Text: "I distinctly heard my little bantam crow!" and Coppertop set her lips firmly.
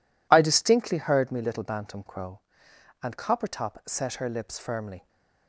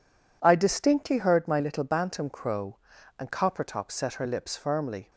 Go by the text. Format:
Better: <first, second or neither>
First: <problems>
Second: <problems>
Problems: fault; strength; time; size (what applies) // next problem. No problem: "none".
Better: second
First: says "me" for "my"; at 1.3 s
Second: none